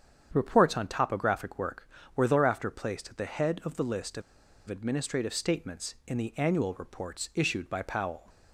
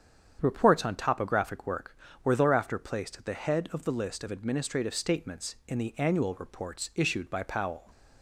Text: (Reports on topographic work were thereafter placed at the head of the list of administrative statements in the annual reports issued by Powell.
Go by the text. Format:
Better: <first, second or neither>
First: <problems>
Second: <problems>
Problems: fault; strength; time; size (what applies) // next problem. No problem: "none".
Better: second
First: starts louder than the rest; strong; until 1.3 s; 8 dB // pauses between "of" and "administrative"; noticeable; at 4.2 s; 0.46 s long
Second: starts louder than the rest; strong; until 1.4 s; 8 dB